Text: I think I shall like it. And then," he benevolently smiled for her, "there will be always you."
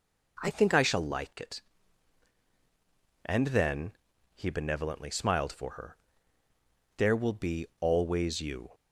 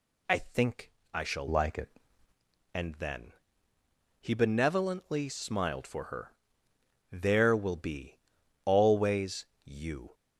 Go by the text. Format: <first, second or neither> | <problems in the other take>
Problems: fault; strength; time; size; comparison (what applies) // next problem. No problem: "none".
first | pauses between "think" and "I"; slight; at 0.9 s; 0.22 s long // changes voice from "like" to "it"; from 1.4 to 1.9 s; 0.5 s long // pauses between "be" and "always"; noticeable; at 8.1 s; 0.48 s long // pauses between "always" and "you"; slight; at 9.4 s; 0.20 s long